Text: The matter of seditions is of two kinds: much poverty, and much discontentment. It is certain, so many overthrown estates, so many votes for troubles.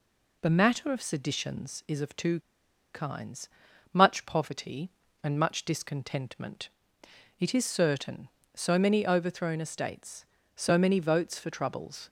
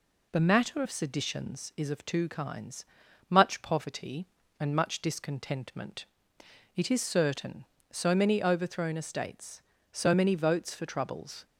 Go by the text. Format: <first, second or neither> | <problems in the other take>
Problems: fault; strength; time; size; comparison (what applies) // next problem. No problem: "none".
second | pauses between "two" and "kinds"; noticeable; at 2.3 s; 0.55 s long